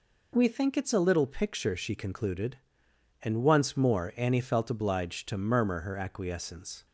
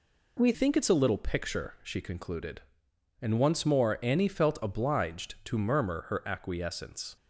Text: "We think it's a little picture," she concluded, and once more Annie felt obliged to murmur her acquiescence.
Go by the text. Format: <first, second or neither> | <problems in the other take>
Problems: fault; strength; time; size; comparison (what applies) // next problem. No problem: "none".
first | changes voice at "think"; from 0.5 s on; 6.6 s long